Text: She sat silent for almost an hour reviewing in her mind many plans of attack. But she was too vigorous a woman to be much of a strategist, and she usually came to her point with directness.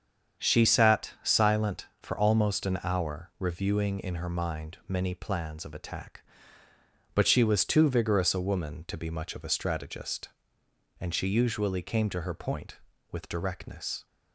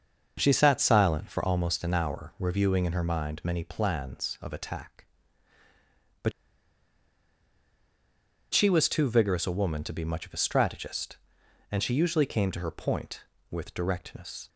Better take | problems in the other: first | starts louder than the rest; until 1.3 s; 6 dB; strong in the first // pauses between "But" and "she"; strong; at 6.3 s; 2.2 s long

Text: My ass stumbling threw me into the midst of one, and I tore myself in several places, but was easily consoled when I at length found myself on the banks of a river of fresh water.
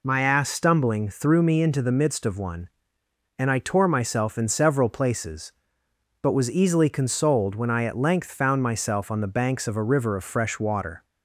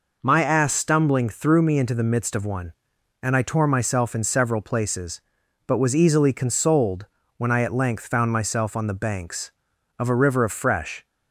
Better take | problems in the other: first | pauses between "consoled" and "when"; slight; at 7.0 s; 0.32 s long // stops before "water"; at 11.0 s

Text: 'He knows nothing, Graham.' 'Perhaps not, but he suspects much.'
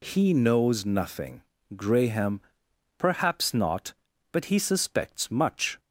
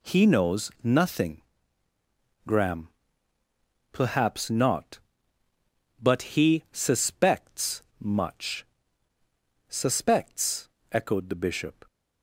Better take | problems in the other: first | pauses between "suspects" and "much"; slight; at 7.8 s; 0.16 s long // goes on to say "Suspects echoed the bishop"; strong; from 9.6 s on; 2.1 s long

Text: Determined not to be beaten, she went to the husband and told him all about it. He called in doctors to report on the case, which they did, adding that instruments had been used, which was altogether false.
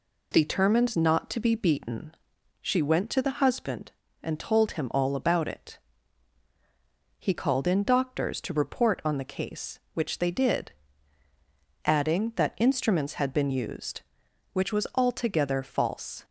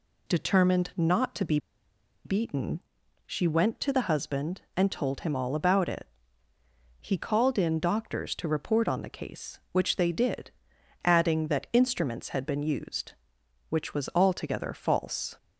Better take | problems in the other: first | pauses between "be" and "beaten"; noticeable; at 1.5 s; 0.67 s long

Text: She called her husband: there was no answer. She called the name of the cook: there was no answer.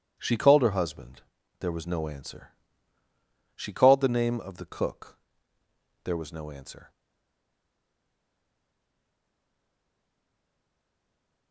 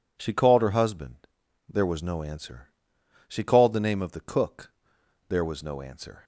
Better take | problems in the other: second | stays silent after the last word; strong; from 6.9 s on; 4.6 s long

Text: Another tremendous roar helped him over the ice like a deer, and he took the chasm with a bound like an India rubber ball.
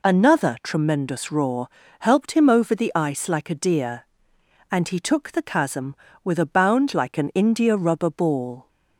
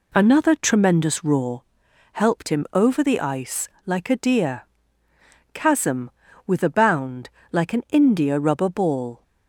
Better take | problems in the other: first | pauses between "roar" and "helped"; noticeable; at 1.6 s; 0.50 s long; slight in the first // pauses between "ice" and "like"; slight; at 3.6 s; 0.20 s long // skips "and he took the"; at 5.0 s // pauses between "bound" and "like"; slight; at 7.3 s; 0.20 s long

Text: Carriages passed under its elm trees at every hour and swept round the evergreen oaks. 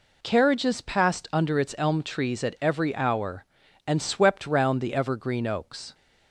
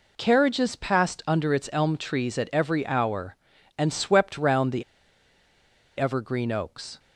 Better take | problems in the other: first | pauses between "the" and "evergreen"; at 4.8 s; 1.1 s long

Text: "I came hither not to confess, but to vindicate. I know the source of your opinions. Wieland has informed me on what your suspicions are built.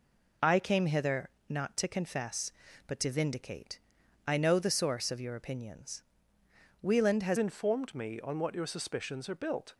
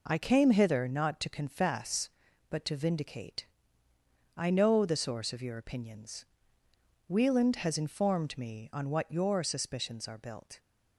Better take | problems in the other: second | pauses between "hither" and "not"; slight; at 1.2 s; 0.18 s long // changes voice at "informed"; from 7.3 s on; 2.4 s long

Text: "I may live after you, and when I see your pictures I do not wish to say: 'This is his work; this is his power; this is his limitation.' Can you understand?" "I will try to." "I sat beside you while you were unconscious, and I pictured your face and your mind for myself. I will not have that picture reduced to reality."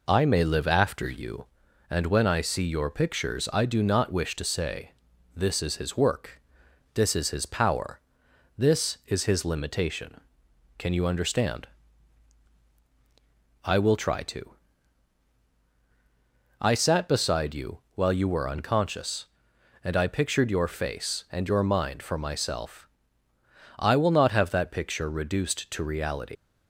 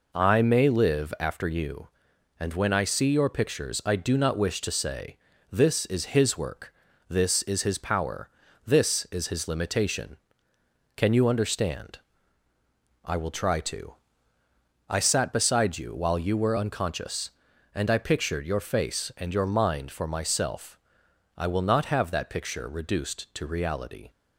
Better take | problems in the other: second | leaves "reality" unfinished; at 26.3 s; 125 ms

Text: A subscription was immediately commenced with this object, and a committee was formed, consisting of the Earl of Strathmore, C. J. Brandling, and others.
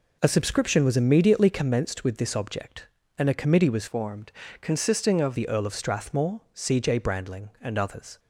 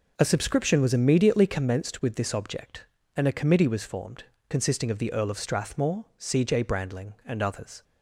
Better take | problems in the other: second | changes voice from "formed" to "of"; from 3.8 to 5.3 s; 1.5 s long

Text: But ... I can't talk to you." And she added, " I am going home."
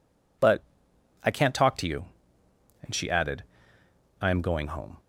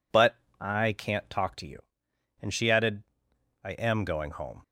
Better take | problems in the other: neither | none

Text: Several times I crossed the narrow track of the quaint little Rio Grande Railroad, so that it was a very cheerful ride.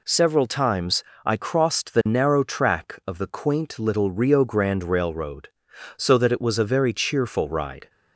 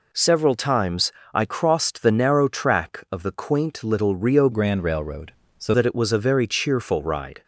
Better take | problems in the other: first | pauses between "times" and "I"; slight; at 1.1 s; 0.22 s long; slight in the first // changes voice from "Grande" to "so"; from 4.5 to 5.7 s; 1.2 s long

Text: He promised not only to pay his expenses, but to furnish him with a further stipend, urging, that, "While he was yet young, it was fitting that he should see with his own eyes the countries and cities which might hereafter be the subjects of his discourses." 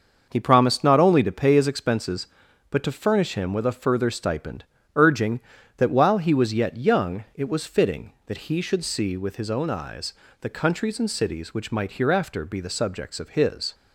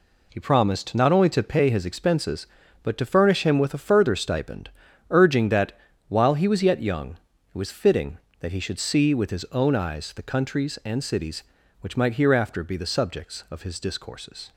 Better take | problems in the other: second | starts louder than the rest; noticeable; until 1.3 s; 6 dB // pauses between "eyes" and "the"; slight; at 10.1 s; 0.30 s long // stops before "discourses"; at 13.7 s

